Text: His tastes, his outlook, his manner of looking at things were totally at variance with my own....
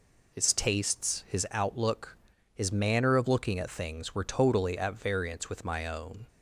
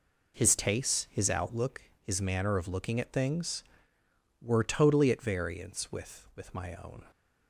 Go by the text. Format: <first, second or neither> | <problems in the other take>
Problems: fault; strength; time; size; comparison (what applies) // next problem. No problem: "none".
first | says "with" twice; at 6.3 s